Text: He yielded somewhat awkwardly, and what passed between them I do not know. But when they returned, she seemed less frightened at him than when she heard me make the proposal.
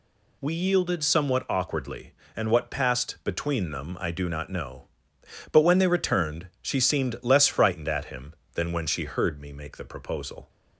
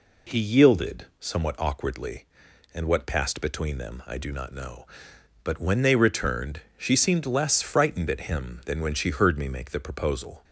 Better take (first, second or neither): second